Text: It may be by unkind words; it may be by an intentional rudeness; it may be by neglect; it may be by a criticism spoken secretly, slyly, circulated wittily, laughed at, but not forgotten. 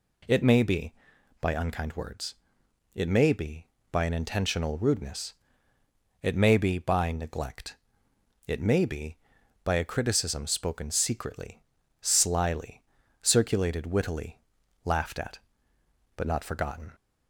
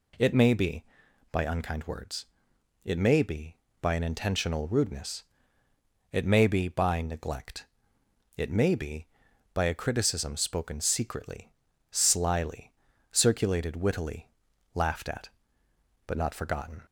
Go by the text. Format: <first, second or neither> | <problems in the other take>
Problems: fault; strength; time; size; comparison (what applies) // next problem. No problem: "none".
neither | none